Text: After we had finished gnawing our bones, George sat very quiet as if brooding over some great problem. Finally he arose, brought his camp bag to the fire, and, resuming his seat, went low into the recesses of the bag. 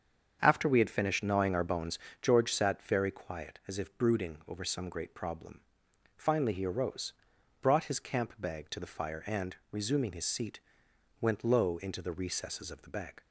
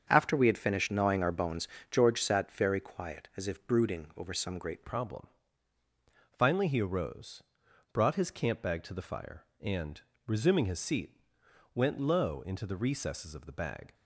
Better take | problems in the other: first | starts louder than the rest; strong; until 1.1 s; 7.5 dB; strong in the first // changes voice at "problem"; from 4.8 s on; 9.1 s long

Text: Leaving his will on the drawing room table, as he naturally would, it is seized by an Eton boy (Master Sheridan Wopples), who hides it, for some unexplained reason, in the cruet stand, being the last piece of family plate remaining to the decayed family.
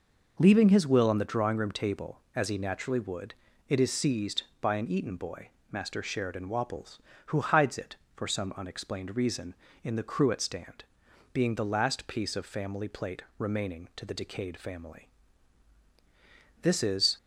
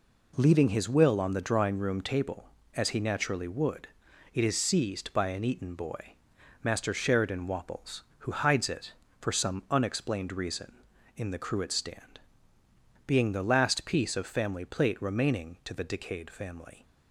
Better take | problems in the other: second | pauses between "plate" and "remaining"; slight; at 13.2 s; 0.16 s long // goes on to say "This is"; from 16.6 s on; 0.56 s long

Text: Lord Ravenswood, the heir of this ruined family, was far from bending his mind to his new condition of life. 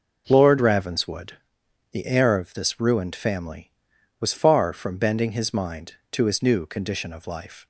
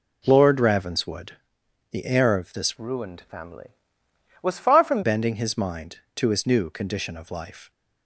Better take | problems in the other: first | changes voice from "ruined" to "from"; from 2.7 to 5.0 s; 2.3 s long

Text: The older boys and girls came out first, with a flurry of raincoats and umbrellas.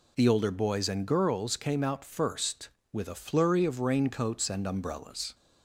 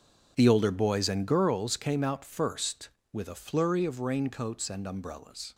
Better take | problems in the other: first | gets quieter; strong; throughout; 14 dB

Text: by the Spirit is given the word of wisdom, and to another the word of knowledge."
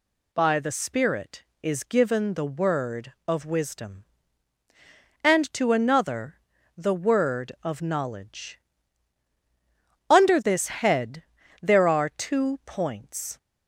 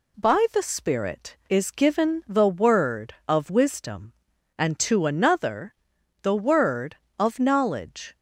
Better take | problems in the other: second | pauses between "another" and "the"; at 6.3 s; 0.40 s long; noticeable in the second // goes on to say "Under this head there are two points"; strong; from 10.0 s on; 3.2 s long

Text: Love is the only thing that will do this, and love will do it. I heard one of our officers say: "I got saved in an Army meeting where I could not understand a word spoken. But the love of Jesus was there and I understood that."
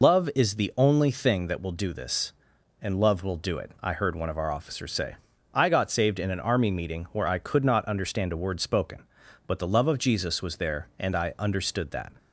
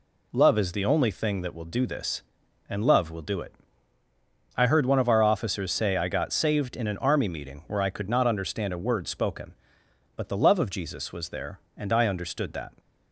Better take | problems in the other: second | loses the start of "Love"; at 0.0 s; 115 ms

